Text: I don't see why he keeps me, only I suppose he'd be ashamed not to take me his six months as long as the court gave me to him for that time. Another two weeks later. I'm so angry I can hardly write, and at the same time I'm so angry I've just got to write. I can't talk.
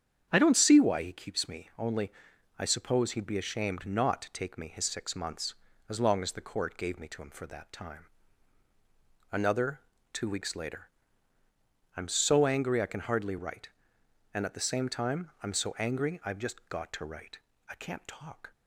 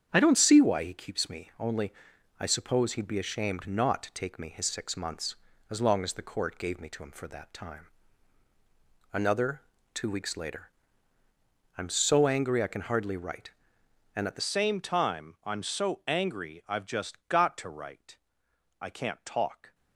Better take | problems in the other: first | starts louder than the rest; strong; until 1.1 s; 8.5 dB; strong in the first // pauses between "only" and "I"; noticeable; at 1.9 s; 0.48 s long; noticeable in the first // pauses between "Another" and "two"; slight; at 9.6 s; 0.32 s long; slight in the first // changes voice at "same"; from 14.4 s on; 5.3 s long

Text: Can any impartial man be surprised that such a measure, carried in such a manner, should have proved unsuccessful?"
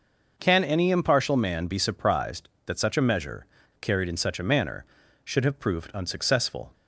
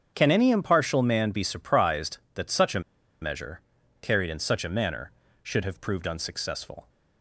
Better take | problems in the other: first | starts louder than the rest; strong; until 1.1 s; 7.5 dB // pauses between "a" and "measure"; at 2.7 s; 0.41 s long

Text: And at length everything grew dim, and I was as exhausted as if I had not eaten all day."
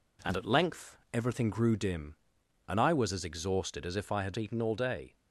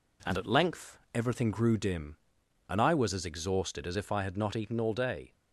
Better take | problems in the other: second | pauses between "length" and "everything"; slight; at 0.9 s; 0.16 s long; slight in the second // skips "not"; at 4.3 s

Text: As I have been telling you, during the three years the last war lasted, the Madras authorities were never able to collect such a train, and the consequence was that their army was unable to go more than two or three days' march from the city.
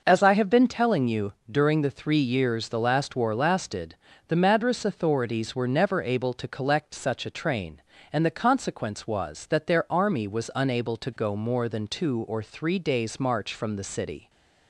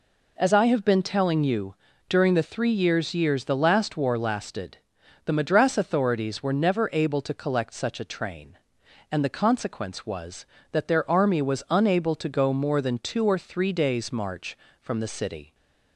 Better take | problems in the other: first | says "years" twice; at 3.1 s

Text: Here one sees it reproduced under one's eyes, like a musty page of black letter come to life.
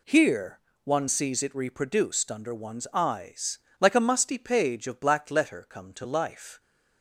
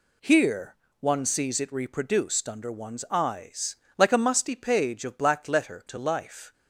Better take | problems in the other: first | pauses between "Here" and "one"; slight; at 0.7 s; 0.24 s long; slight in the first // skips "come"; at 5.8 s

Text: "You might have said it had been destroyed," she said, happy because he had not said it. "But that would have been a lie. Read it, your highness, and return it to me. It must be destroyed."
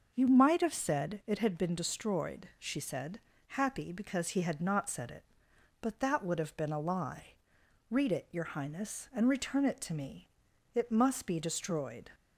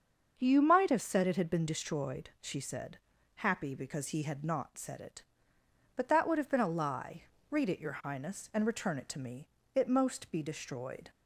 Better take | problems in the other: first | starts louder than the rest; until 1.3 s; 6.5 dB; noticeable in the first // says "most" for "must"; at 9.8 s

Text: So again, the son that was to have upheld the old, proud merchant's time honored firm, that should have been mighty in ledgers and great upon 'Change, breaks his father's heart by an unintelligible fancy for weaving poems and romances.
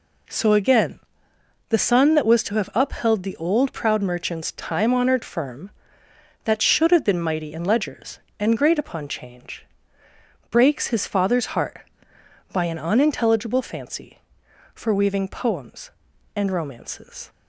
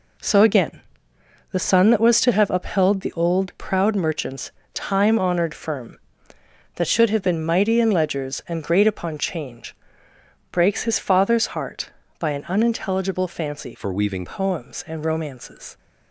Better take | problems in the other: first | pauses between "merchant's" and "time"; slight; at 4.5 s; 0.24 s long // changes voice from "for" to "weaving"; from 13.7 to 14.2 s; 0.5 s long

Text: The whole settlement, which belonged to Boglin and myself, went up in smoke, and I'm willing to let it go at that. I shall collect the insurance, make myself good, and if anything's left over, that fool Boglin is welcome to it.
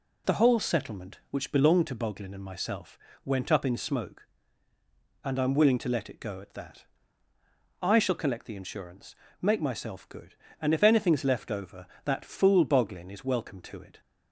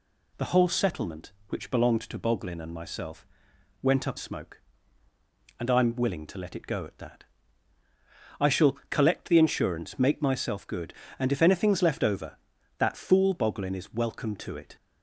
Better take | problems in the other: first | skips "in"; at 4.1 s

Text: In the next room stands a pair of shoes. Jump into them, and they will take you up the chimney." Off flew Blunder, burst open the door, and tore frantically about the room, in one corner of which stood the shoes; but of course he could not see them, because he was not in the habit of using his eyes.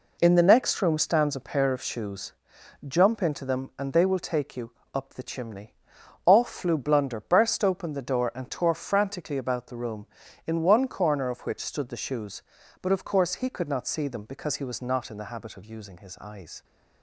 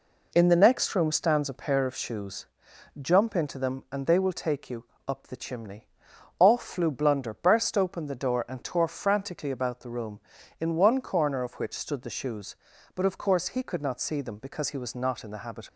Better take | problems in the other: first | pauses between "you" and "up"; slight; at 4.8 s; 0.22 s long; slight in the first // stops before "of using his eyes"; at 15.6 s

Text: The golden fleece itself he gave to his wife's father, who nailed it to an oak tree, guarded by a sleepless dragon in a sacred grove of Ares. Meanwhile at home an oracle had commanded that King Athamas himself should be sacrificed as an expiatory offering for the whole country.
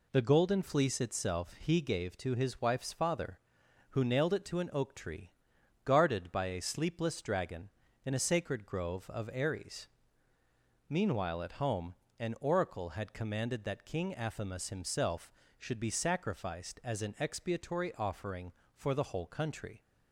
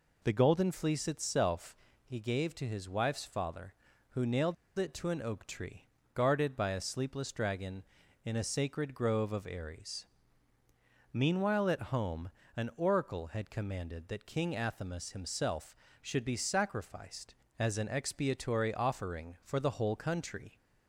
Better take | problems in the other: first | pauses between "itself" and "he"; slight; at 1.7 s; 0.28 s long // pauses between "nailed" and "it"; slight; at 4.5 s; 0.24 s long // pauses between "home" and "an"; slight; at 12.2 s; 0.26 s long; slight in the first

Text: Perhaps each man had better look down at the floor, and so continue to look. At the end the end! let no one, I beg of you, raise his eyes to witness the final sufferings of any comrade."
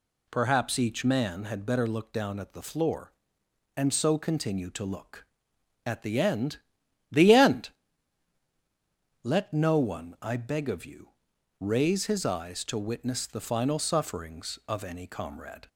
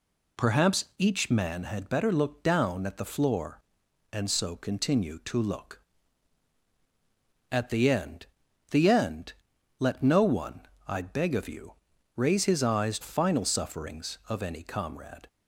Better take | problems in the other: first | pauses between "end" and "the"; at 8.2 s; 0.44 s long; noticeable in the first // skips "to witness the"; at 12.9 s

